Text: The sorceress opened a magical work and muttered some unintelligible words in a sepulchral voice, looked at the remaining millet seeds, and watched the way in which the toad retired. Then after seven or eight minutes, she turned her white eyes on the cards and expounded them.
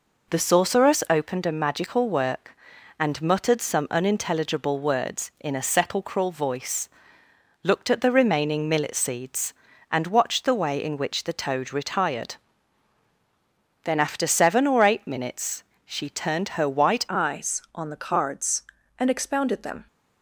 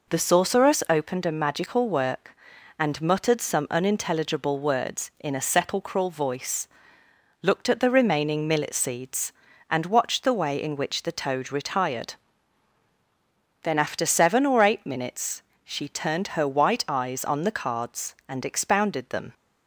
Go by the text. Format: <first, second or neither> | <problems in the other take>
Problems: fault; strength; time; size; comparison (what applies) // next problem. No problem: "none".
second | changes voice at "eyes"; from 17.0 s on; 2.8 s long